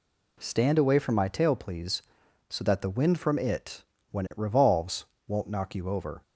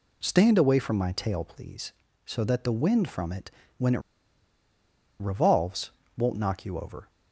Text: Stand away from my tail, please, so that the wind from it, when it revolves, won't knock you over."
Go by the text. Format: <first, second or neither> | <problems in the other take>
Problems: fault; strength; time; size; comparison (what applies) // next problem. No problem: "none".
first | pauses between "it" and "revolves"; at 4.0 s; 1.1 s long